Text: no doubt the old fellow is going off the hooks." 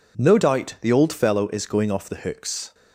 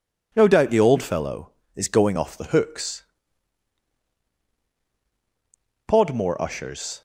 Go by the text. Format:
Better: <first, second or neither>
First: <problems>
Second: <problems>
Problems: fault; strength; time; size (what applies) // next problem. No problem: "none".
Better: first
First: none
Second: goes on to say "Podmore ushers"; noticeable; from 5.8 s on; 1.1 s long